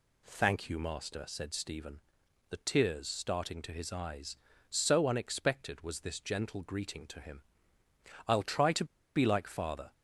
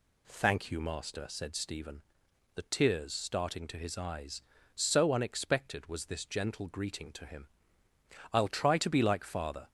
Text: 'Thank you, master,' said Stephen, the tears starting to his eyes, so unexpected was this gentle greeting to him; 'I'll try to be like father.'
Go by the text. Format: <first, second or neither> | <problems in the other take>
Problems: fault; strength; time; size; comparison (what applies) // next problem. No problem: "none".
second | pauses between "to" and "be"; slight; at 8.8 s; 0.31 s long